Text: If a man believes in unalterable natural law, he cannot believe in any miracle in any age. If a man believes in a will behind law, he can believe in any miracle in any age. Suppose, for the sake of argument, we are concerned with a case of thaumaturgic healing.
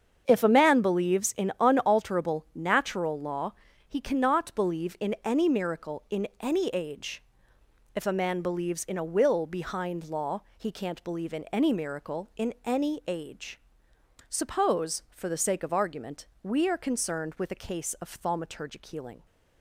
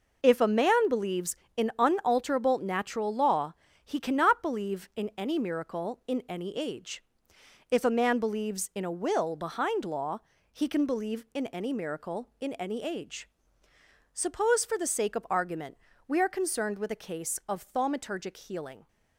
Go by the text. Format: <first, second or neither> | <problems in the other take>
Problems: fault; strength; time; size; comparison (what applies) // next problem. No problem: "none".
second | starts louder than the rest; strong; until 1.2 s; 7.5 dB // says "can't" for "can"; at 10.7 s